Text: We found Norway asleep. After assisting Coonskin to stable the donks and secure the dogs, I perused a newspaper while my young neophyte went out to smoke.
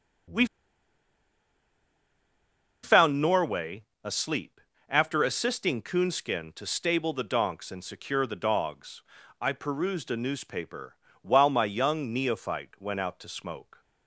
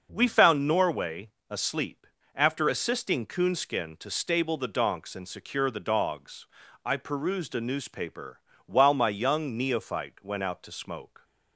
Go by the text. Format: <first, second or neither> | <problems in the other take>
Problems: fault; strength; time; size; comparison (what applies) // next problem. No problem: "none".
second | starts louder than the rest; until 3.7 s; 6 dB; also in the second // pauses between "We" and "found"; strong; at 0.4 s; 2.3 s long // pauses between "Norway" and "asleep"; slight; at 3.8 s; 0.20 s long; slight in the second // pauses between "newspaper" and "while"; slight; at 10.9 s; 0.24 s long; slight in the second